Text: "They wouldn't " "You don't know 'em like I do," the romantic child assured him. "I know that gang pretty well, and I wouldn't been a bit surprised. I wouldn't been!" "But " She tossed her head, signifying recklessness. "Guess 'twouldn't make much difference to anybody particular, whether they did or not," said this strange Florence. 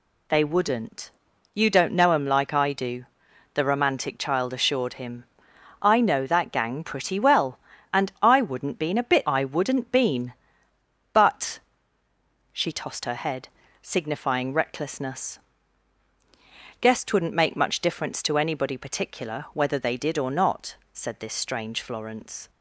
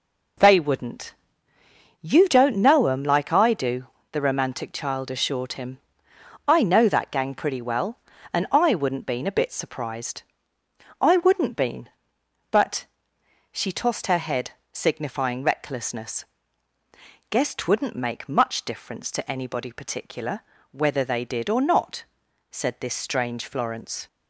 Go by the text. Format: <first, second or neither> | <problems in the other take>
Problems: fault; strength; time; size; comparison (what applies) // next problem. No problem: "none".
second | skips "surprised"; at 9.2 s